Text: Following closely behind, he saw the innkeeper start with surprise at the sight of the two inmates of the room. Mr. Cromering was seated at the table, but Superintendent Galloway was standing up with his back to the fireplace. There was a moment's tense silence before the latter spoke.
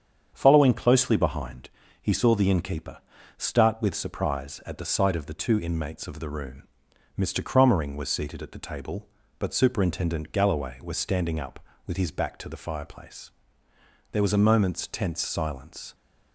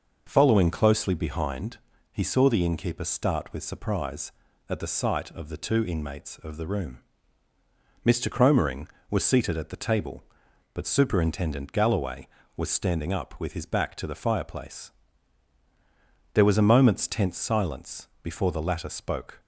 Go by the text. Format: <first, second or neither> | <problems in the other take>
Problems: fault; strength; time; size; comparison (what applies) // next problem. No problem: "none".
second | starts louder than the rest; strong; until 1.3 s; 7.5 dB // pauses between "innkeeper" and "start"; at 2.9 s; 0.40 s long // stops before "before the latter spoke"; at 15.9 s